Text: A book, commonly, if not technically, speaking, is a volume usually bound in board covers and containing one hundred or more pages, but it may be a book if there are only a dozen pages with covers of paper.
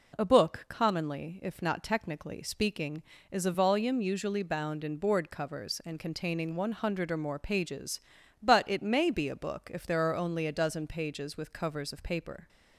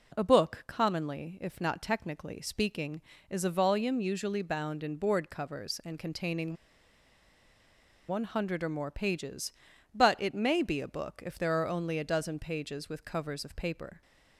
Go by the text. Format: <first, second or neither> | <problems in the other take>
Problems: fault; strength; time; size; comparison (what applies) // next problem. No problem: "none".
first | pauses between "containing" and "one"; strong; at 6.5 s; 1.5 s long